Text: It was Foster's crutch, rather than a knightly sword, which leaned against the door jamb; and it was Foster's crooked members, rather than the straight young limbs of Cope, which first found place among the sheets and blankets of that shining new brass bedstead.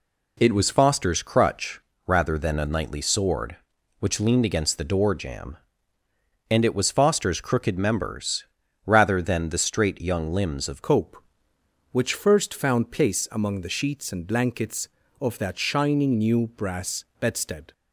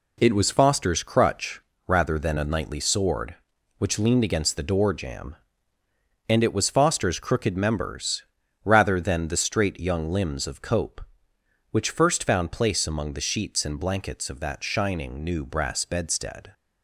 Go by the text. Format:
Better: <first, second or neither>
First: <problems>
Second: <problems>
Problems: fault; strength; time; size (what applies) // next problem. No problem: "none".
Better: second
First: changes voice at "Cope"; from 10.8 s on; 6.9 s long // pauses between "brass" and "bedstead"; slight; at 17.0 s; 0.16 s long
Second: none